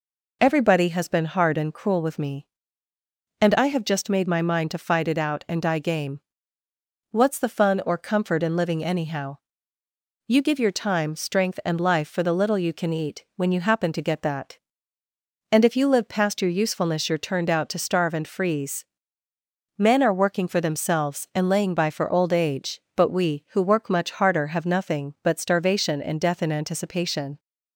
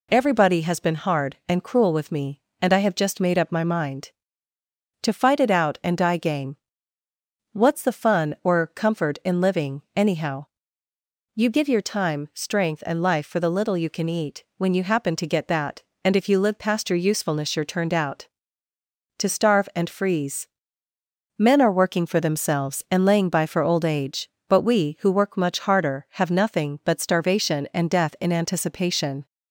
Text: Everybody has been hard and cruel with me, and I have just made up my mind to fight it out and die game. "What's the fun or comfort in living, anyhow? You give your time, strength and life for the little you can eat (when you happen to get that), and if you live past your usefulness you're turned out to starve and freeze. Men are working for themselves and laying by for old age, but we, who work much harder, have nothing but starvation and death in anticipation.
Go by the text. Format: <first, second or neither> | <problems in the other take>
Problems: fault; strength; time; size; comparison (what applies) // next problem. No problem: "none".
second | skips "up"; at 4.2 s